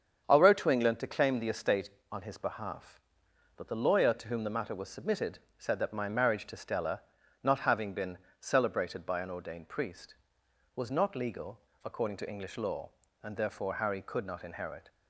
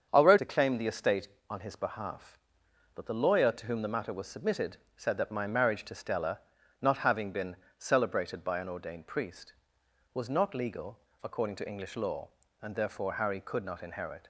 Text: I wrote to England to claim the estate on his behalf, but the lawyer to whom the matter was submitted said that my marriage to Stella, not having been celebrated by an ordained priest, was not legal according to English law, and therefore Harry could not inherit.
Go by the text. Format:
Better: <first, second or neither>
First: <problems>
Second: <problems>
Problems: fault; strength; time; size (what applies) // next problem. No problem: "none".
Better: first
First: starts louder than the rest; strong; until 1.2 s; 7.5 dB // pauses between "submitted" and "said"; slight; at 5.3 s; 0.20 s long // pauses between "been" and "celebrated"; slight; at 8.1 s; 0.24 s long // pauses between "legal" and "according"; slight; at 11.5 s; 0.24 s long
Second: starts louder than the rest; strong; until 1.1 s; 7.5 dB // skips "to England"; at 0.3 s // pauses between "submitted" and "said"; slight; at 4.7 s; 0.20 s long // pauses between "been" and "celebrated"; slight; at 7.5 s; 0.24 s long // pauses between "legal" and "according"; slight; at 10.9 s; 0.24 s long